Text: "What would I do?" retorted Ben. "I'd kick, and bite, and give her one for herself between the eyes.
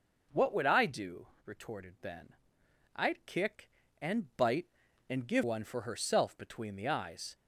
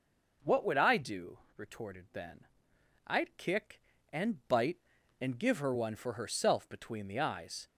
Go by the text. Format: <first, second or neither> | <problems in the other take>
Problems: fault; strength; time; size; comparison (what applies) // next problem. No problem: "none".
second | skips "her"; at 5.4 s